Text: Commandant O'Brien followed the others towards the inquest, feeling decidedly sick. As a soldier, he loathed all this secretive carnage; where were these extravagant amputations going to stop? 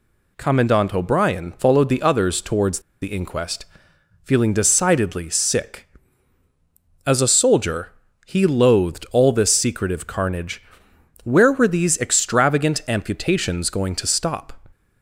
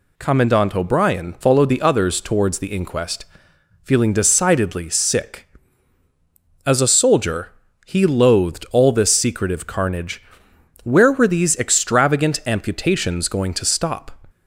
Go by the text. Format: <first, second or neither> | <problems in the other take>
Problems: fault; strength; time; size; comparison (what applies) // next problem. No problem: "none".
second | pauses between "towards" and "the"; slight; at 2.8 s; 0.21 s long